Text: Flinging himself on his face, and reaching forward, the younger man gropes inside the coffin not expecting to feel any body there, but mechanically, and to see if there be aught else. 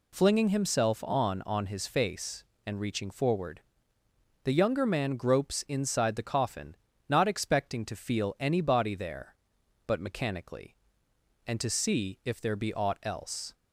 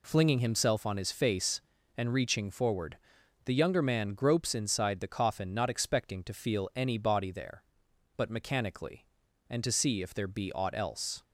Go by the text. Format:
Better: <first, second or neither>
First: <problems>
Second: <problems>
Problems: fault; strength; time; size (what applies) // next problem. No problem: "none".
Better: second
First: says "on" twice; at 1.4 s // pauses between "coffin" and "not"; slight; at 6.7 s; 0.34 s long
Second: none